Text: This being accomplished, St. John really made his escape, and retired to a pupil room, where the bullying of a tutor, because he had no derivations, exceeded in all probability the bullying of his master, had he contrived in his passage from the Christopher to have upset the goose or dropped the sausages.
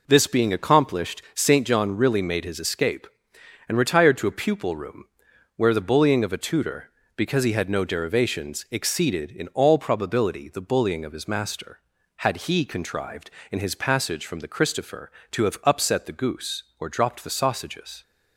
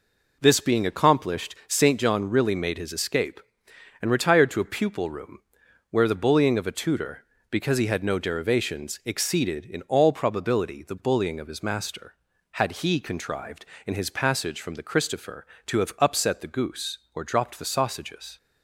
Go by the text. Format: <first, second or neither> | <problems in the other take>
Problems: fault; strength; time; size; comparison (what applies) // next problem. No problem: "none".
neither | none